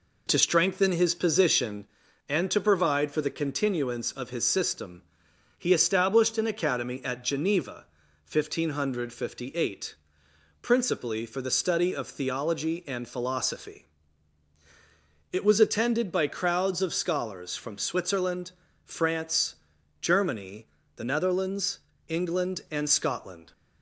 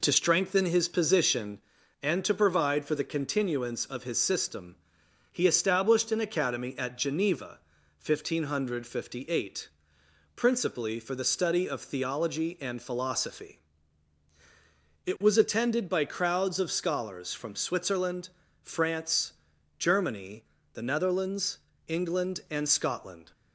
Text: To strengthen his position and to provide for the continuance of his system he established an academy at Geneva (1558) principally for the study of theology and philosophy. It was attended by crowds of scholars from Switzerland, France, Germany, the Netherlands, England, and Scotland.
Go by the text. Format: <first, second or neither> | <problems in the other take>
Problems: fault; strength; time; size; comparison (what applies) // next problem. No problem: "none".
neither | pauses between "system" and "he"; noticeable; the same in both